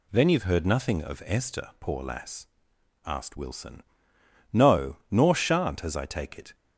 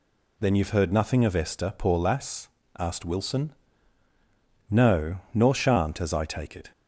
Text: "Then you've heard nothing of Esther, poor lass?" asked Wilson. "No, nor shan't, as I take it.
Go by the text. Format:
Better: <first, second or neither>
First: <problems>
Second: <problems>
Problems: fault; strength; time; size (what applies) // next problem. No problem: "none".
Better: neither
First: none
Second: none